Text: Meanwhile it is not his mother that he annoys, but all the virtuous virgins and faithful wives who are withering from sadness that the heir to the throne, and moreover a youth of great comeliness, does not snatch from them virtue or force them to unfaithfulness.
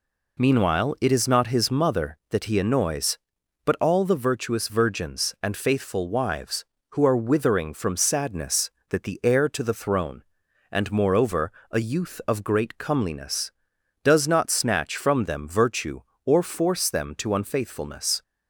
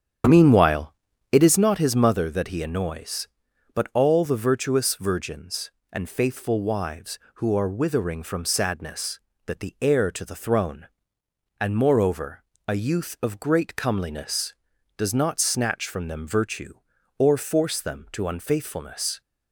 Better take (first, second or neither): first